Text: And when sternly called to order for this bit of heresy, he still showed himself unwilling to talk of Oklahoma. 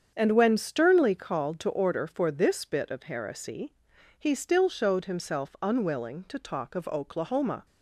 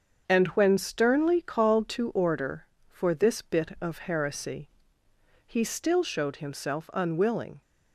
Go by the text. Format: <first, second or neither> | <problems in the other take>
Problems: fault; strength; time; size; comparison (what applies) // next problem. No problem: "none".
first | starts louder than the rest; until 1.2 s; 7 dB; strong in the first // stops before "to talk of Oklahoma"; at 7.6 s